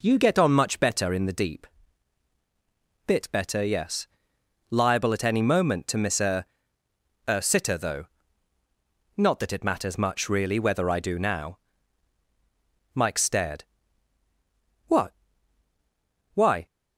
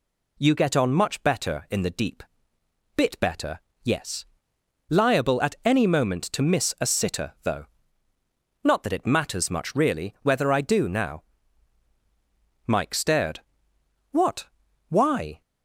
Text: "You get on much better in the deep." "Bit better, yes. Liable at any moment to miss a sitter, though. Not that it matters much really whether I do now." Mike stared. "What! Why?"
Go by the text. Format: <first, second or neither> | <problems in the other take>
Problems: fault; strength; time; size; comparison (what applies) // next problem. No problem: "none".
second | says "a" twice; at 7.2 s